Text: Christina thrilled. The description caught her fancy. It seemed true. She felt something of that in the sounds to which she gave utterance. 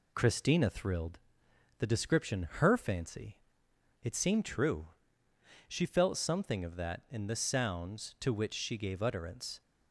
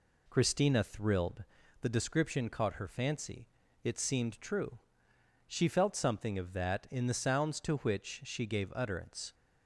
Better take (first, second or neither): second